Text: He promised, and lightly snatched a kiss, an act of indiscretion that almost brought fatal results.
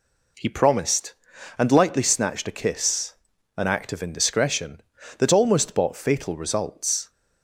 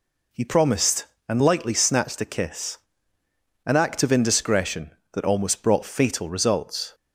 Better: second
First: says "bought" for "brought"; at 5.7 s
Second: none

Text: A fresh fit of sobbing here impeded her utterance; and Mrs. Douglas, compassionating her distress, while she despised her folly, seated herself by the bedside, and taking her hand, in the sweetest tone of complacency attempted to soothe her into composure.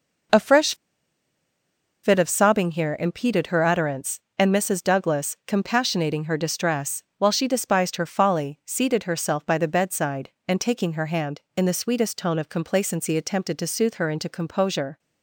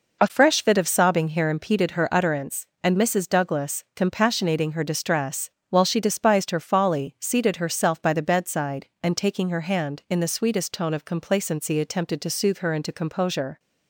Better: second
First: pauses between "fresh" and "fit"; strong; at 0.7 s; 1.2 s long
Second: none

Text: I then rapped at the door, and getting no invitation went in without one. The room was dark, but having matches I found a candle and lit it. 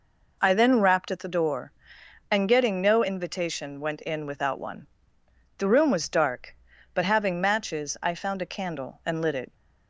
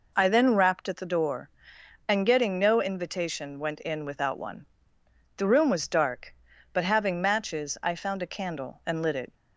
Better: neither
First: none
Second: none

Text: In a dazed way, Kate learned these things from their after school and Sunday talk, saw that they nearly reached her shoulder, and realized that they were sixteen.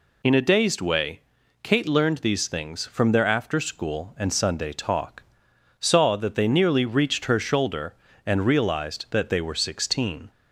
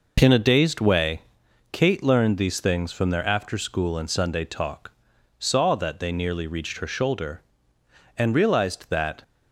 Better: first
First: none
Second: stops before "they were sixteen"; at 9.2 s

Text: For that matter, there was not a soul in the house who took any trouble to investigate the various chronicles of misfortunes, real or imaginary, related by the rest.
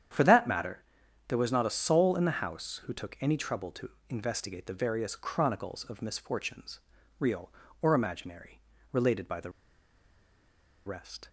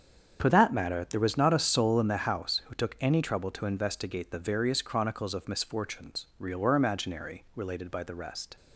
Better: second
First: starts louder than the rest; strong; until 1.5 s; 9 dB // pauses between "to" and "investigate"; slight; at 3.8 s; 0.22 s long // pauses between "the" and "rest"; strong; at 9.4 s; 1.3 s long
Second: starts louder than the rest; strong; until 1.4 s; 7.5 dB

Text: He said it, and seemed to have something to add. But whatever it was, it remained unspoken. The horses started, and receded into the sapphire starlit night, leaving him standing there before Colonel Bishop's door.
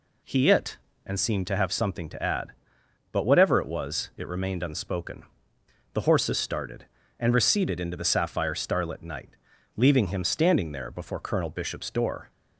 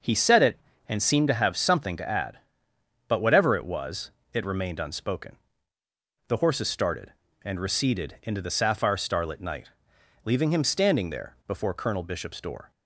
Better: second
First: skips "said"; at 0.4 s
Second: none

